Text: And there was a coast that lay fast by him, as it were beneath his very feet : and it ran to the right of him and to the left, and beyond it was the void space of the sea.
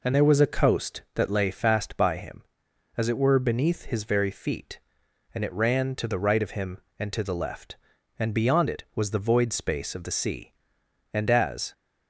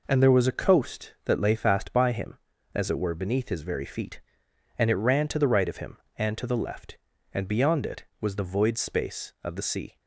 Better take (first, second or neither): second